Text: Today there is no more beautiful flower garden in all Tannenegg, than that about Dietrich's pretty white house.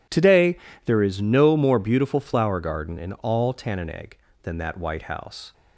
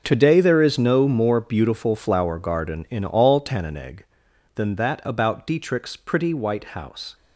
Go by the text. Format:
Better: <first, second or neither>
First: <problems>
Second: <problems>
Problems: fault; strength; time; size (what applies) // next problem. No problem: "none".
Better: second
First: pauses between "Today" and "there"; slight; at 0.5 s; 0.30 s long // skips "about Dietrich's pretty"; at 4.7 s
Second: none